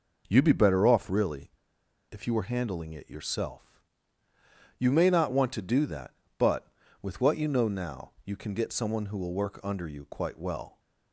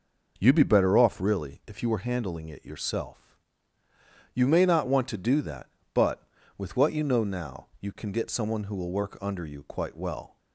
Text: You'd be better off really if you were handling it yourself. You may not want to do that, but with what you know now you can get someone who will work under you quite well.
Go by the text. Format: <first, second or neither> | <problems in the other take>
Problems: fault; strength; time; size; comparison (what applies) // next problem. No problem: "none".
second | pauses between "really" and "if"; noticeable; at 1.4 s; 0.61 s long